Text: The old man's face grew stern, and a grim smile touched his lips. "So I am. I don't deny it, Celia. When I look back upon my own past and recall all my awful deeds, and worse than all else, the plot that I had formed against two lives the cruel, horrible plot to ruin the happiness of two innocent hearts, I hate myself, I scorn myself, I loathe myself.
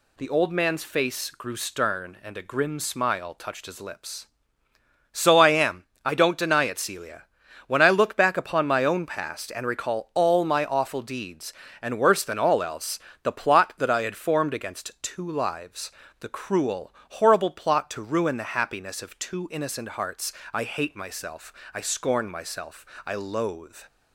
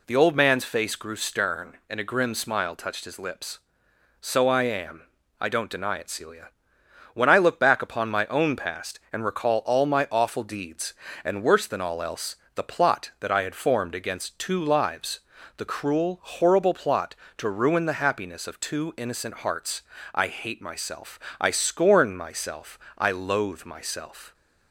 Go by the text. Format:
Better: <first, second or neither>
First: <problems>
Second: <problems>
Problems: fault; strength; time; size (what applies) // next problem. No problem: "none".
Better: second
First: pauses between "lives" and "the"; slight; at 15.9 s; 0.30 s long // stops before "myself"; at 23.8 s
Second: pauses between "lives" and "the"; at 15.1 s; 0.38 s long